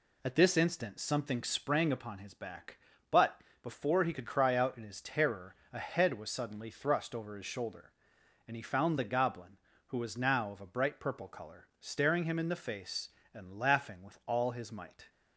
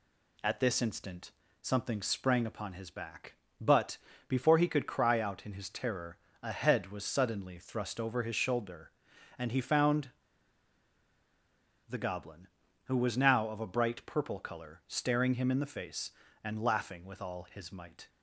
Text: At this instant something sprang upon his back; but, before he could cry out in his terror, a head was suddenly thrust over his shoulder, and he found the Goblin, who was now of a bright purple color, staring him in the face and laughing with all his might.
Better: first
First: none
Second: pauses between "instant" and "something"; slight; at 1.3 s; 0.30 s long // pauses between "found" and "the"; strong; at 10.1 s; 1.7 s long

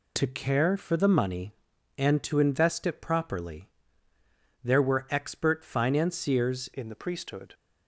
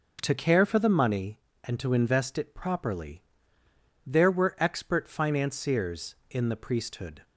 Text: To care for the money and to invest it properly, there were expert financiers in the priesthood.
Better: second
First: changes voice at "in"; from 6.7 s on; 0.8 s long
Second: none

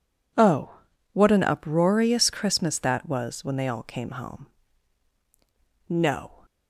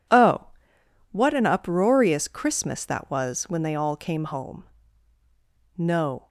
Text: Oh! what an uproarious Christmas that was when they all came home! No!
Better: neither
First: none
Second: none

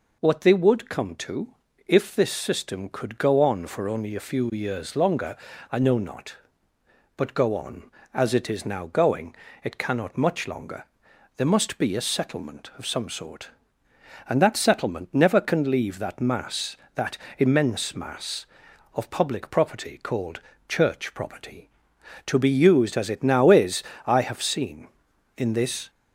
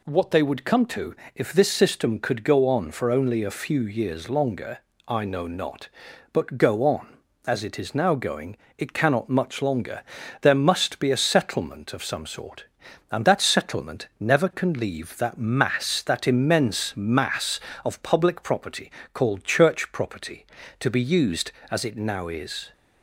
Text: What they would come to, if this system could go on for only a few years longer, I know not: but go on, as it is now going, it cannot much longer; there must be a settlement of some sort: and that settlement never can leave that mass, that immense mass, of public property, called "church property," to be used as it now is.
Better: second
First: pauses between "that" and "immense"; slight; at 17.1 s; 0.22 s long // pauses between "called" and "church"; slight; at 20.3 s; 0.28 s long // goes on to say "I have seen in this"; strong; from 24.0 s on; 1.8 s long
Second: none

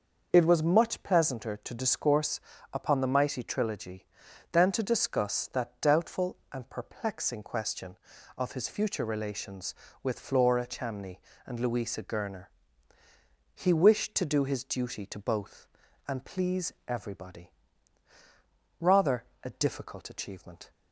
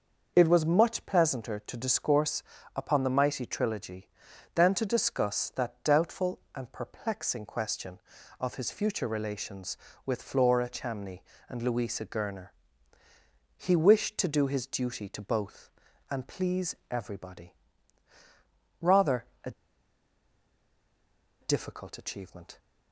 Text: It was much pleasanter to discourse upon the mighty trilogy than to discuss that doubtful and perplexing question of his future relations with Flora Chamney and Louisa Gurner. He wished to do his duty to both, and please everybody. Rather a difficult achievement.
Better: first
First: starts louder than the rest; until 1.3 s; 6 dB // pauses between "discourse" and "upon"; slight; at 2.3 s; 0.34 s long // pauses between "Rather" and "a"; slight; at 19.2 s; 0.18 s long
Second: starts louder than the rest; until 1.3 s; 6 dB // pauses between "discourse" and "upon"; slight; at 2.4 s; 0.34 s long // pauses between "Rather" and "a"; slight; at 19.2 s; 0.18 s long // pauses between "a" and "difficult"; strong; at 19.5 s; 1.8 s long

